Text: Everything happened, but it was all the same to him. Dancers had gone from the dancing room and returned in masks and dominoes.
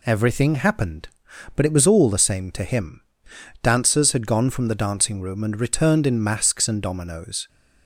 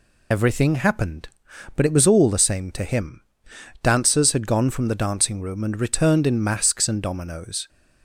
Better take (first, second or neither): first